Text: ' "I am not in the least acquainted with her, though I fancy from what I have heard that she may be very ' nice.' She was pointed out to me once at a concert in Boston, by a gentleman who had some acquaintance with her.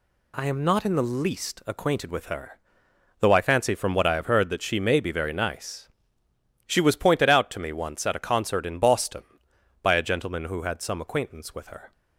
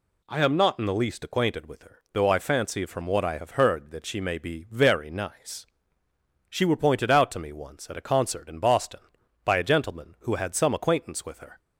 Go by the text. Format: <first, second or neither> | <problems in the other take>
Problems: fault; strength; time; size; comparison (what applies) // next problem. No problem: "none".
first | says "were" for "was"; at 6.6 s